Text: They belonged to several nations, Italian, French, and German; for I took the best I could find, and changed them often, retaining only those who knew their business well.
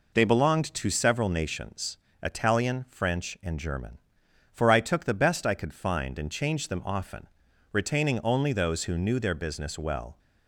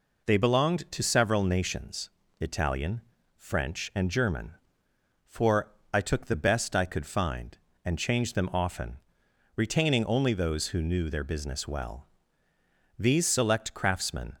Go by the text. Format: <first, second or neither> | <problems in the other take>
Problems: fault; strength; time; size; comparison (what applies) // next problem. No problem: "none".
first | pauses between "for" and "I"; slight; at 5.7 s; 0.22 s long // goes on to say "These select craftsmen"; from 12.9 s on; 1.4 s long